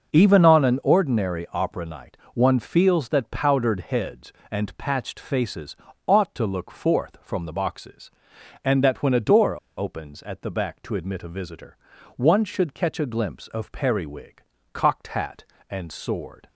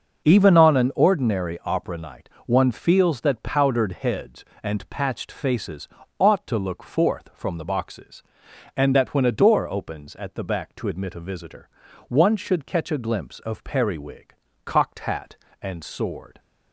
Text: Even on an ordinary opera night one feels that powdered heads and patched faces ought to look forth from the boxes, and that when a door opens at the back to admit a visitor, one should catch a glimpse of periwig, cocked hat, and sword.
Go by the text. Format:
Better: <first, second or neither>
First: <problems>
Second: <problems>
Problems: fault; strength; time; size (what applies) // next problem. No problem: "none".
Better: second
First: pauses between "night" and "one"; slight; at 2.1 s; 0.16 s long // pauses between "faces" and "ought"; slight; at 5.7 s; 0.32 s long // pauses between "door" and "opens"; slight; at 9.5 s; 0.20 s long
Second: pauses between "night" and "one"; slight; at 2.2 s; 0.16 s long // pauses between "faces" and "ought"; slight; at 5.8 s; 0.32 s long